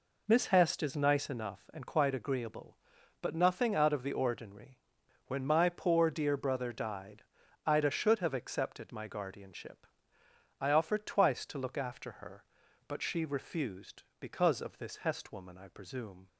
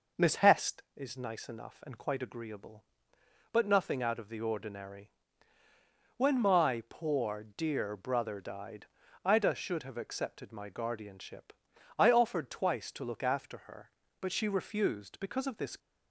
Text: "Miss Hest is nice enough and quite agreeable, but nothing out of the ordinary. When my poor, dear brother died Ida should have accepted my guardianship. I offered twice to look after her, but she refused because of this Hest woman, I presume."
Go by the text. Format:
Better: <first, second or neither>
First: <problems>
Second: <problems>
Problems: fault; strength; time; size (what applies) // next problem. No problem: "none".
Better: first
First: pauses between "died" and "Ida"; at 7.2 s; 0.42 s long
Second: pauses between "died" and "Ida"; at 8.8 s; 0.38 s long // stops before "Hest woman I presume"; at 15.7 s